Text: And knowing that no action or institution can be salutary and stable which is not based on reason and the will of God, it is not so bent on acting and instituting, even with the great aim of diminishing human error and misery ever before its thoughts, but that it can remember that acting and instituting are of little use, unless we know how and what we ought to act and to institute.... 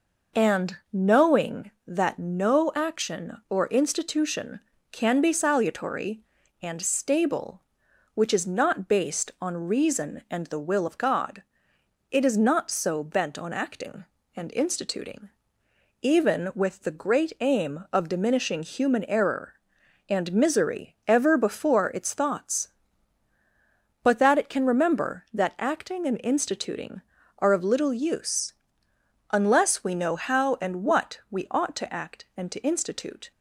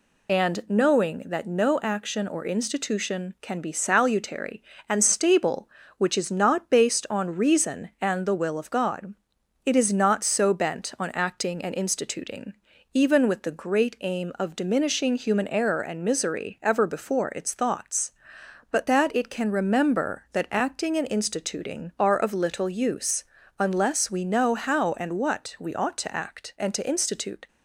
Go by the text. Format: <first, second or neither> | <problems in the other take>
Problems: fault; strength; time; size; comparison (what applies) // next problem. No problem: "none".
first | loses the start of "And"; at 0.2 s; 40 ms